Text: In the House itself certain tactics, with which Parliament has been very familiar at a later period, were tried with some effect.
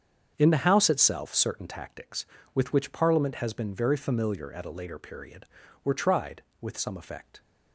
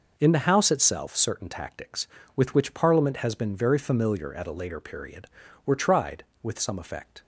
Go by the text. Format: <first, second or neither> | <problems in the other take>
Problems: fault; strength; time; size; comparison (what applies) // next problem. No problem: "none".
second | starts louder than the rest; strong; until 1.8 s; 7.5 dB